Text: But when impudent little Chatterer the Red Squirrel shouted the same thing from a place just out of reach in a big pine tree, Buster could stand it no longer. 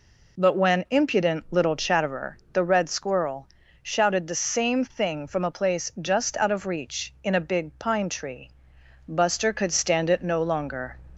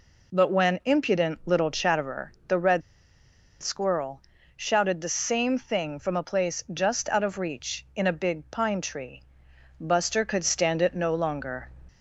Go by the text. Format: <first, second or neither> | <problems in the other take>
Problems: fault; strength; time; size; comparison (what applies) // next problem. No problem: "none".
first | pauses between "Chatterer" and "the"; slight; at 2.3 s; 0.16 s long; slight in the first // pauses between "Red" and "Squirrel"; noticeable; at 2.8 s; 0.79 s long // pauses between "Squirrel" and "shouted"; slight; at 4.2 s; 0.34 s long; slight in the first